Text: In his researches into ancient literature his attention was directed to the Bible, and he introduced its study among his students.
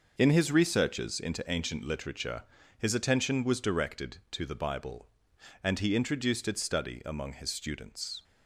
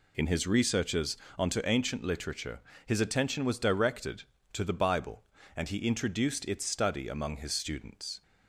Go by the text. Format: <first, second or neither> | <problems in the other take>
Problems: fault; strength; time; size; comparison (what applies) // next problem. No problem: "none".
first | says "onto" for "into"; at 1.3 s // pauses between "literature" and "his"; slight; at 2.5 s; 0.26 s long; slight in the first